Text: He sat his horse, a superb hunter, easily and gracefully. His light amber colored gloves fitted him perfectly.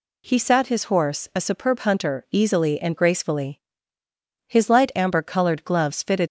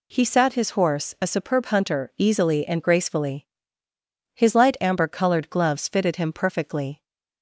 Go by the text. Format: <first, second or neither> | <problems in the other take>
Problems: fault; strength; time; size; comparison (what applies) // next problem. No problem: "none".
second | stops before "him perfectly"; at 6.2 s